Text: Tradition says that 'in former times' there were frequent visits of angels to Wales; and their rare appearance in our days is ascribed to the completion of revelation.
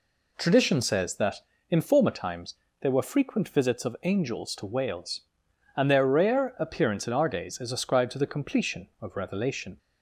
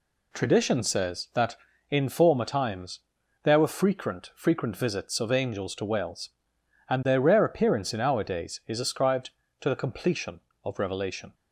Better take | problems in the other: first | pauses between "times" and "there"; at 3.0 s; 0.42 s long; slight in the first // says "frequent" twice; at 4.3 s

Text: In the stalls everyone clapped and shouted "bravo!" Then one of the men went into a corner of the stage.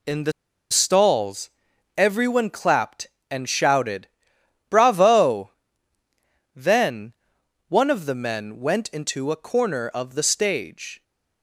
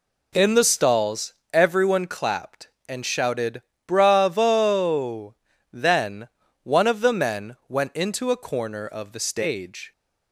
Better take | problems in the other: second | pauses between "the" and "stalls"; at 0.3 s; 0.38 s long // pauses between "stalls" and "everyone"; noticeable; at 1.5 s; 0.48 s long; slight in the second // pauses between "shouted" and "bravo"; noticeable; at 4.0 s; 0.64 s long; slight in the second // pauses between "Then" and "one"; noticeable; at 7.1 s; 0.56 s long; slight in the second

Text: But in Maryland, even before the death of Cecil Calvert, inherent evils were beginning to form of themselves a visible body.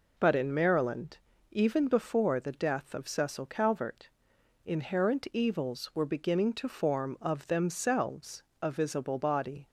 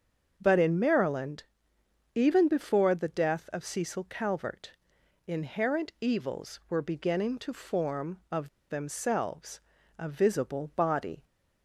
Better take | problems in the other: first | starts louder than the rest; until 1.3 s; 6.5 dB // pauses between "of" and "themselves"; slight; at 8.4 s; 0.21 s long // pauses between "themselves" and "a"; at 9.5 s; 0.40 s long; slight in the first

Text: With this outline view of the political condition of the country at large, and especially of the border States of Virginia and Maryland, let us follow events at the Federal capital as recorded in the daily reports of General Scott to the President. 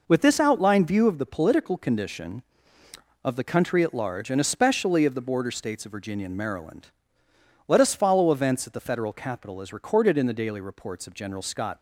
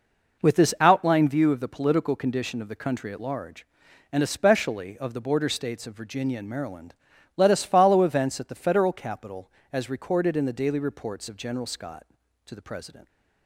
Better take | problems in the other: second | stops before "to the President"; at 11.7 s

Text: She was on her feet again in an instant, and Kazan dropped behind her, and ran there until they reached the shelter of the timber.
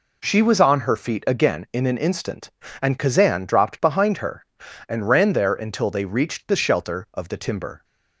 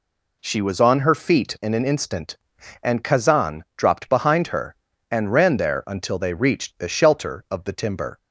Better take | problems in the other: first | skips "again"; at 1.5 s

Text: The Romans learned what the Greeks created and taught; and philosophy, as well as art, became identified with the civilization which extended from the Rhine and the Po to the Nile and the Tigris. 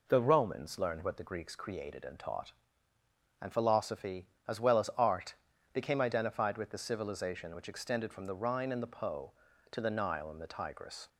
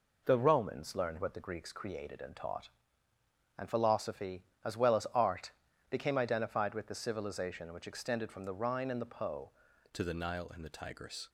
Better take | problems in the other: first | changes voice at "to"; from 9.9 s on; 1.3 s long

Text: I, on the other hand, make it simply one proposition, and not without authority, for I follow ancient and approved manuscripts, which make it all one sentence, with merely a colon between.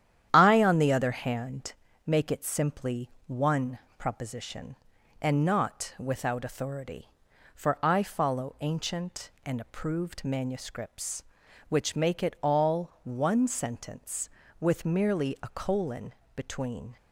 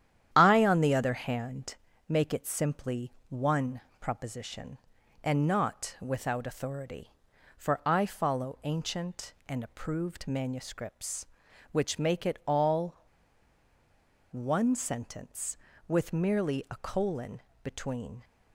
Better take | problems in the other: first | starts louder than the rest; strong; until 1.3 s; 10 dB; strong in the first // pauses between "simply" and "one"; slight; at 3.1 s; 0.18 s long; slight in the first // pauses between "one" and "proposition"; slight; at 3.8 s; 0.18 s long; slight in the first // pauses between "all" and "one"; strong; at 12.9 s; 1.3 s long // pauses between "colon" and "between"; slight; at 17.3 s; 0.22 s long; slight in the first

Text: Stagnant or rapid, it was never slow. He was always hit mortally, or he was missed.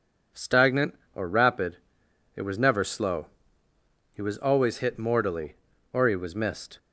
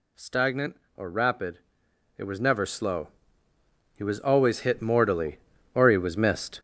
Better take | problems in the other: first | gets louder; throughout; 7 dB

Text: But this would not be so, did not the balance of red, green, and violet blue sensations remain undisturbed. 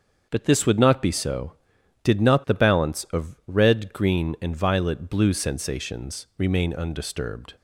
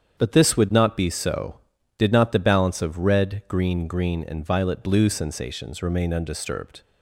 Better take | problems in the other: first | starts louder than the rest; strong; until 1.2 s; 8 dB; also in the first // says "green" twice; at 3.8 s

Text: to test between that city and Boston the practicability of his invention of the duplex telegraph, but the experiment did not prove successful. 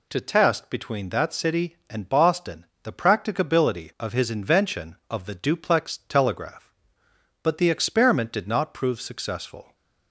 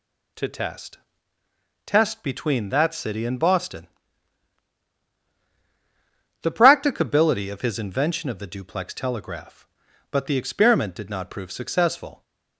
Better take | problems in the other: first | says "test" twice; at 1.8 s // pauses between "Boston" and "the"; strong; at 3.8 s; 2.5 s long; slight in the first

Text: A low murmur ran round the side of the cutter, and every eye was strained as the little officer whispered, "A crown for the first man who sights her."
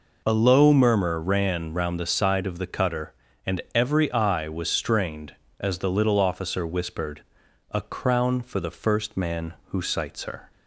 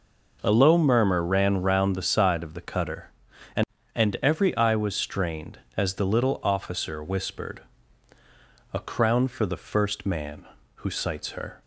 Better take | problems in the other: first | says "and" twice; at 3.9 s

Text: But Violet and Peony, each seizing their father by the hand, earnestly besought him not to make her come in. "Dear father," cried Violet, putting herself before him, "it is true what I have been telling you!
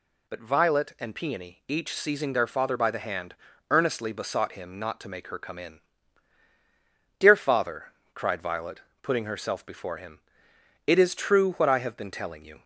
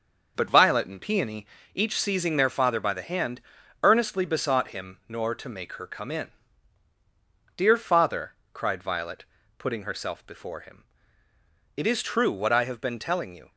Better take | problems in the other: first | starts louder than the rest; until 1.3 s; 6 dB // says "nor" for "not"; at 5.0 s

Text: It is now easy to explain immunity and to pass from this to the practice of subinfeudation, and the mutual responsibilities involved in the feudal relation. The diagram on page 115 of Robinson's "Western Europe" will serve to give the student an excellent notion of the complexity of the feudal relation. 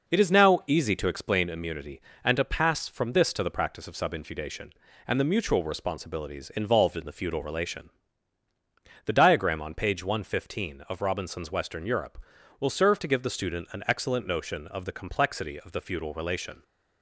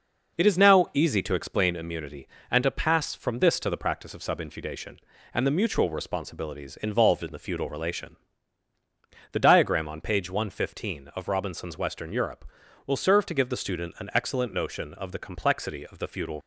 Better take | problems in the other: first | stops before "relation"; at 16.4 s

